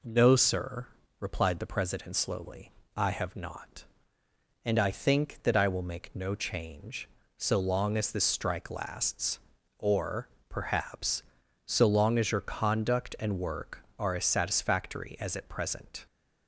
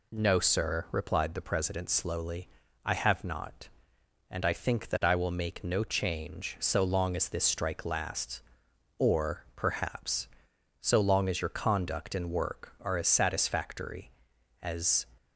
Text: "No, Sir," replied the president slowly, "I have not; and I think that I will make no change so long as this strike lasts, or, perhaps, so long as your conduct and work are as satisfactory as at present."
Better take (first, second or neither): first